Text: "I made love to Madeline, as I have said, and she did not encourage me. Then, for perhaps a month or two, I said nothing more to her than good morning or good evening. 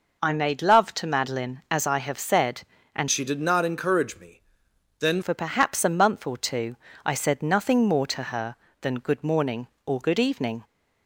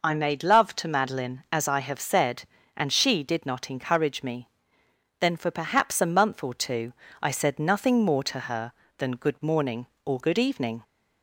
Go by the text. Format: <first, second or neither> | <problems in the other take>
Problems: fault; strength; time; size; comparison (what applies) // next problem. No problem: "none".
second | changes voice from "she" to "Then"; from 3.1 to 5.2 s; 2.1 s long